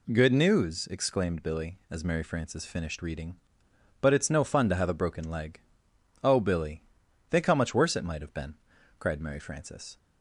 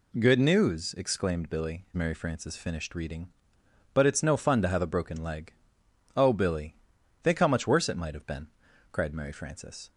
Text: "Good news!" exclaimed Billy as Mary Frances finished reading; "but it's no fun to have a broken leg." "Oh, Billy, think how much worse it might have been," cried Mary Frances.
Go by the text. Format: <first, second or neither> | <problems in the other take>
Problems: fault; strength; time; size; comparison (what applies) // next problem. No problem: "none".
first | skips "as"; at 1.9 s